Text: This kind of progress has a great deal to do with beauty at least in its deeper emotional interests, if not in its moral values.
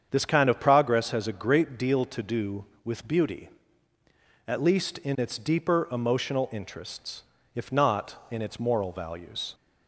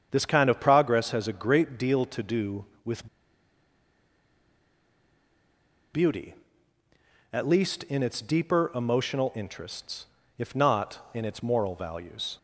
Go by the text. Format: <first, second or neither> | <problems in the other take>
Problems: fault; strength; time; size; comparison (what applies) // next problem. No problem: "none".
first | starts louder than the rest; strong; until 1.1 s; 7.5 dB; strong in the first // pauses between "with" and "beauty"; strong; at 3.0 s; 2.8 s long